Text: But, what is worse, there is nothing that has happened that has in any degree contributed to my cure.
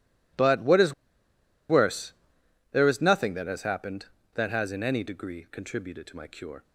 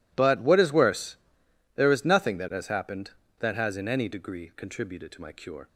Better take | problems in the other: second | pauses between "is" and "worse"; noticeable; at 0.9 s; 0.76 s long

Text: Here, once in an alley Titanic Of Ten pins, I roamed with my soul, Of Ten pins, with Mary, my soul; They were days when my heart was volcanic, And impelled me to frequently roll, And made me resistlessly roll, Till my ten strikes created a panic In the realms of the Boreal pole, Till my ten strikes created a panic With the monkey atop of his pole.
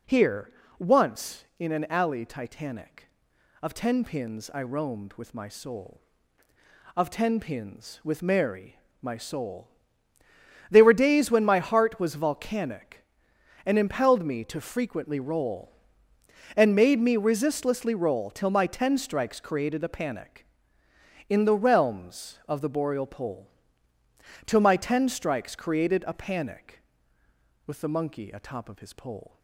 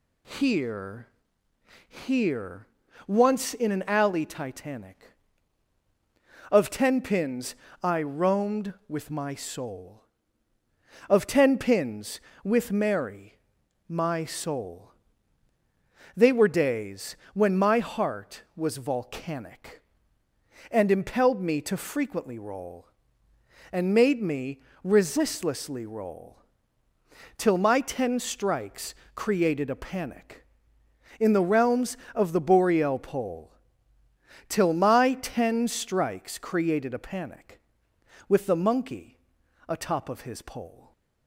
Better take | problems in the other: first | says "Here" twice; at 1.8 s // pauses between "days" and "when"; slight; at 17.1 s; 0.18 s long // pauses between "me" and "resistlessly"; slight; at 24.5 s; 0.24 s long // pauses between "strikes" and "created"; slight; at 28.9 s; 0.20 s long // pauses between "monkey" and "atop"; noticeable; at 39.1 s; 0.48 s long

